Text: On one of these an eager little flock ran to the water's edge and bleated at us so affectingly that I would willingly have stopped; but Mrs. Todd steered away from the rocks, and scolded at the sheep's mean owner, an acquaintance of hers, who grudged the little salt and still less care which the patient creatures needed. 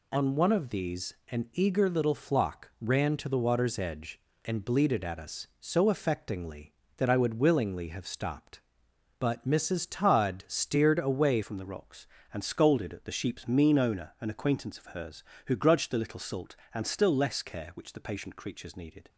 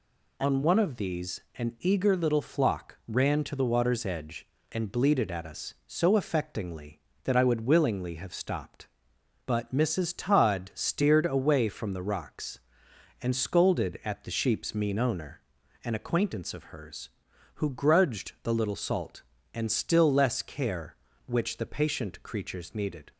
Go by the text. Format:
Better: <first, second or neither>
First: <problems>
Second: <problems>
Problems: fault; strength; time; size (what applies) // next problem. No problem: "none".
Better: second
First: changes voice at "from"; from 11.4 s on; 7.6 s long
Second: none